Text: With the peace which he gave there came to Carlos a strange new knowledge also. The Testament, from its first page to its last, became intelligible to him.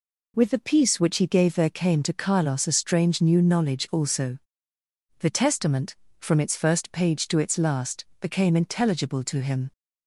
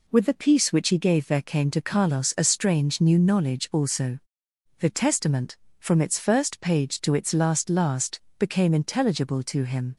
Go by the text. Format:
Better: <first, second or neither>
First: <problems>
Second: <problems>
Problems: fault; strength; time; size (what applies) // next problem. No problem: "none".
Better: first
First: none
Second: says "last" twice; at 7.6 s